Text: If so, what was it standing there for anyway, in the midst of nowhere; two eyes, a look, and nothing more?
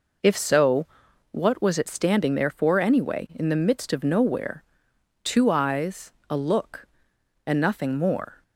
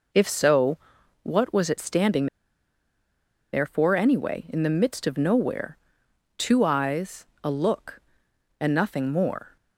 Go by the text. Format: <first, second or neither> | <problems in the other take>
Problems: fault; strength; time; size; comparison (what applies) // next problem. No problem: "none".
first | pauses between "standing" and "there"; strong; at 2.2 s; 1.2 s long